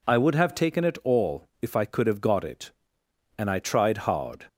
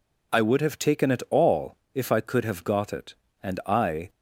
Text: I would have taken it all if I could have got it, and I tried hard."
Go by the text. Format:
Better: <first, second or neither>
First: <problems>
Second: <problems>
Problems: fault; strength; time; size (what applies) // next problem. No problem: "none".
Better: first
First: none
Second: pauses between "all" and "if"; slight; at 1.7 s; 0.20 s long // stops before "tried hard"; at 4.0 s